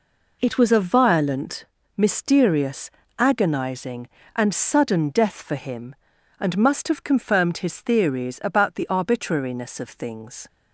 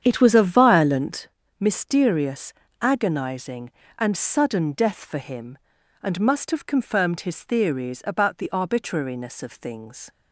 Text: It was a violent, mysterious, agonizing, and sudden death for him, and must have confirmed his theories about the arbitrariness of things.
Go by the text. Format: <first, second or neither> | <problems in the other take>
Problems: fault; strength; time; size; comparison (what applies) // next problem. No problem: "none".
first | starts louder than the rest; strong; until 1.3 s; 8.5 dB